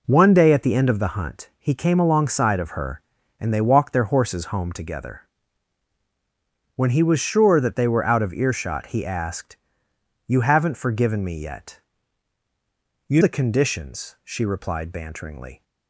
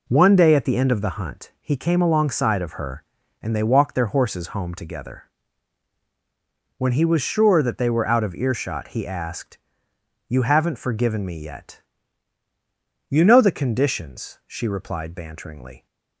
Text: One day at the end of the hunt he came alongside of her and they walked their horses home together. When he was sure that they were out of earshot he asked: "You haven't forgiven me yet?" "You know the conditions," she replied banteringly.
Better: second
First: skips "know"; at 13.2 s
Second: none

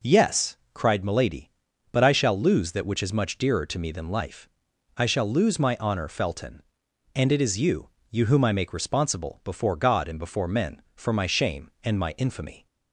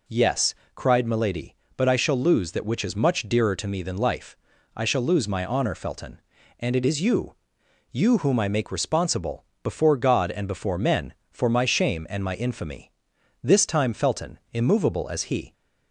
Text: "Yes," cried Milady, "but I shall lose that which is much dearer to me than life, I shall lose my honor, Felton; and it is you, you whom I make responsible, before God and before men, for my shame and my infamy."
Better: first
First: none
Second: goes on to say "This time Felton immovable as he"; strong; from 13.4 s on; 2.1 s long

